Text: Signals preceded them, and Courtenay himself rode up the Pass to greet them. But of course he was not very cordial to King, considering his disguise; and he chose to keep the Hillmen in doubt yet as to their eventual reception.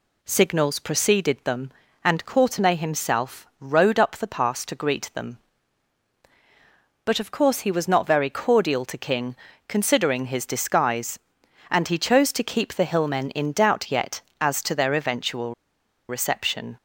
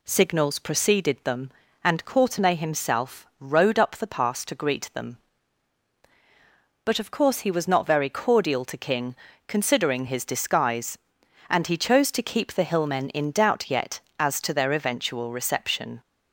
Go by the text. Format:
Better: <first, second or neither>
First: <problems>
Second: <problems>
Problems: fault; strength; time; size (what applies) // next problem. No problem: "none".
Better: second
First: pauses between "eventual" and "reception"; noticeable; at 15.5 s; 0.55 s long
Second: none